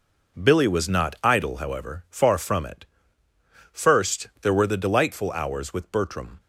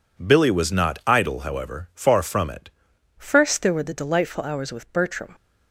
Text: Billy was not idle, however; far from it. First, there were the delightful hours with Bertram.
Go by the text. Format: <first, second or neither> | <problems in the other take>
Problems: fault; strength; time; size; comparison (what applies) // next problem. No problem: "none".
first | changes voice at "First"; from 3.1 s on; 2.2 s long